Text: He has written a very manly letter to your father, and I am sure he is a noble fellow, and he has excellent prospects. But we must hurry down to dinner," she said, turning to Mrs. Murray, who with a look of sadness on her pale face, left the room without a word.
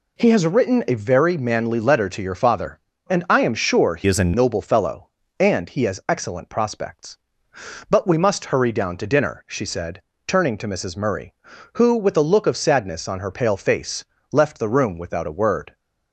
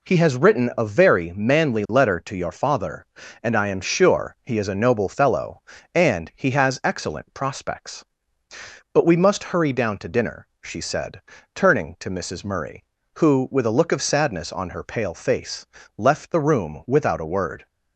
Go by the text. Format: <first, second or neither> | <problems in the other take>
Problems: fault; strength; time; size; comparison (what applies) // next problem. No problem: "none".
second | changes voice from "is" to "a"; from 4.0 to 4.3 s; 0.3 s long